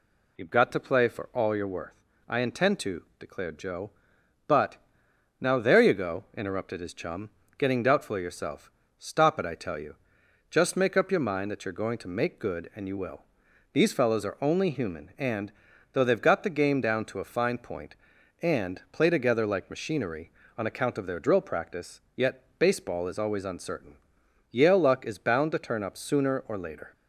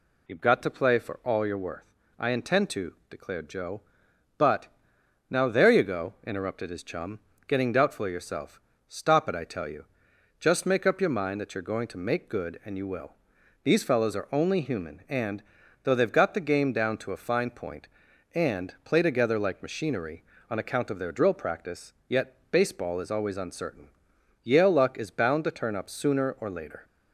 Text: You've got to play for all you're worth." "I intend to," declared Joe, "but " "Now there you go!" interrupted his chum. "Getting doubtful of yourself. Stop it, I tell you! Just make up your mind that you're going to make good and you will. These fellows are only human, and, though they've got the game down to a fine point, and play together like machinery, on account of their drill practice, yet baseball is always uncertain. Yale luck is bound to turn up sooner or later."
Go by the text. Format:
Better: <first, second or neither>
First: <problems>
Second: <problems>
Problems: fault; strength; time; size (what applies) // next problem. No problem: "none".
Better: neither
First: pauses between "yet" and "baseball"; slight; at 22.4 s; 0.16 s long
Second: pauses between "yet" and "baseball"; slight; at 22.3 s; 0.16 s long